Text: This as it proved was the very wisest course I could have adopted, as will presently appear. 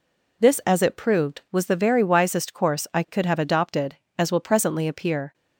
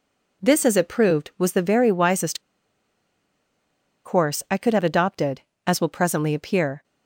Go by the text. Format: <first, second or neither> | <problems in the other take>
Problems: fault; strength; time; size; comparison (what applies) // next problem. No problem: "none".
first | pauses between "wisest" and "course"; strong; at 2.4 s; 1.6 s long